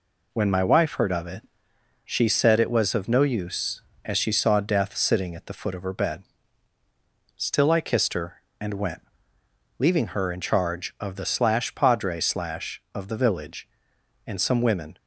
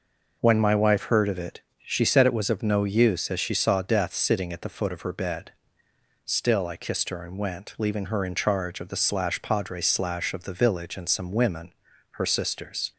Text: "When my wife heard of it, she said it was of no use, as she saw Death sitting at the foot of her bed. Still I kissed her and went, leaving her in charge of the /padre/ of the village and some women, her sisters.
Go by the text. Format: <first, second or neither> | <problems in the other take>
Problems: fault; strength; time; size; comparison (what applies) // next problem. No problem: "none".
second | stops before "her sisters"; at 14.9 s